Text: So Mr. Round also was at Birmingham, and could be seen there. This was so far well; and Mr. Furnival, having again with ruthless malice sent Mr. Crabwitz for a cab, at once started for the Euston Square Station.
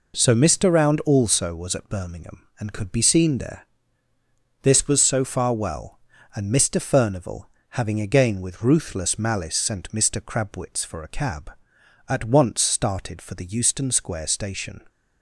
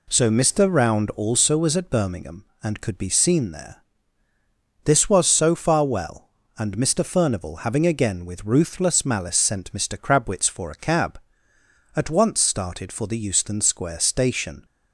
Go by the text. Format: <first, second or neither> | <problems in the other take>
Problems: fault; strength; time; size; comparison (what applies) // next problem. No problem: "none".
neither | none